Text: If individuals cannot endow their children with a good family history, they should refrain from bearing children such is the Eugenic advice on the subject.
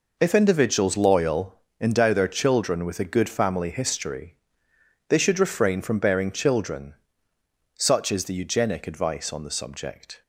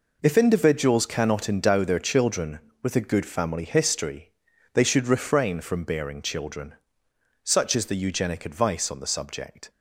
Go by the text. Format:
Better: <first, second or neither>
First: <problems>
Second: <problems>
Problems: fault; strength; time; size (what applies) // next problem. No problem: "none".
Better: second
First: says "loyal" for "cannot"; at 0.9 s // pauses between "children" and "such"; noticeable; at 6.9 s; 0.84 s long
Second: pauses between "children" and "such"; noticeable; at 6.7 s; 0.68 s long